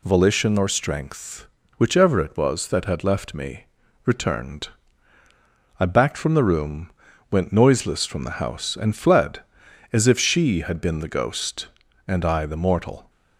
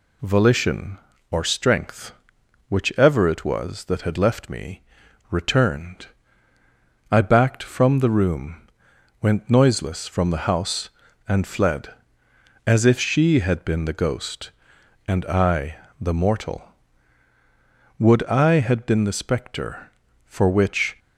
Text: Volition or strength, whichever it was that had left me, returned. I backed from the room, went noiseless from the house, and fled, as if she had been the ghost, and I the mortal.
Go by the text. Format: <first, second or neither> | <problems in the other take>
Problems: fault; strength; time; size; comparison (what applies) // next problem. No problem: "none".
first | pauses between "I" and "the"; slight; at 15.7 s; 0.24 s long // goes on to say "Would I had been the spectre for which"; strong; from 18.0 s on; 2.9 s long